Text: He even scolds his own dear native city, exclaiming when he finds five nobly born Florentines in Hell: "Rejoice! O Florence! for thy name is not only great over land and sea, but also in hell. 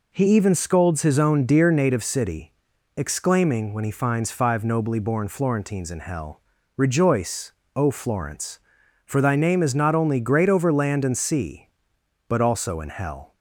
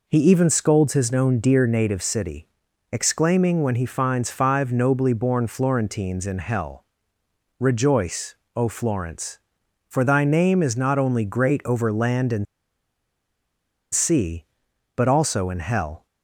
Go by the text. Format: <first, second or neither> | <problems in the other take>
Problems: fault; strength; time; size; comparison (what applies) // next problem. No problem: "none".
first | pauses between "and" and "sea"; strong; at 12.4 s; 1.4 s long